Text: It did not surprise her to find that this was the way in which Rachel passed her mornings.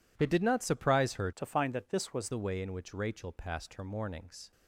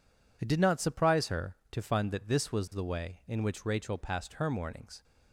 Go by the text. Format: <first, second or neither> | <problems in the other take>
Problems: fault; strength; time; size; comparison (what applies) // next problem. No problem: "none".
second | changes voice from "to" to "was"; from 1.3 to 2.3 s; 1.0 s long